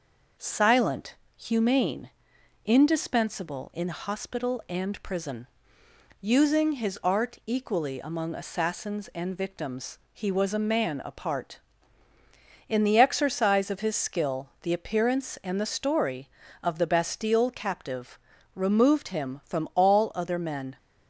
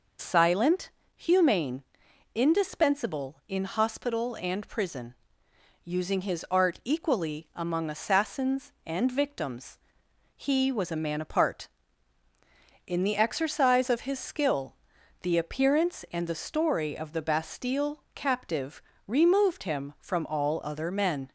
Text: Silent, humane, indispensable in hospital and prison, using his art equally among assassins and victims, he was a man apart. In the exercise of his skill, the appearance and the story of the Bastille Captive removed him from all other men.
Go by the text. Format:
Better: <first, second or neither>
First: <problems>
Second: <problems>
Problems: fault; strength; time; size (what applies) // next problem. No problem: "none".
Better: neither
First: pauses between "Captive" and "removed"; slight; at 18.1 s; 0.34 s long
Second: pauses between "Captive" and "removed"; slight; at 18.8 s; 0.26 s long